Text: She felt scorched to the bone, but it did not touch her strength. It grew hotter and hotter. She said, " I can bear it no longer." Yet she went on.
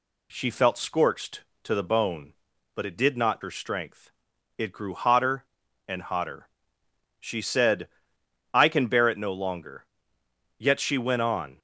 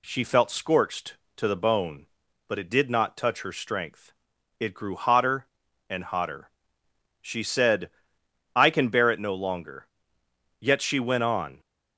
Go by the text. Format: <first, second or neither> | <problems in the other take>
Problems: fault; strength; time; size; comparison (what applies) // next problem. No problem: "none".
second | skips "touch"; at 3.4 s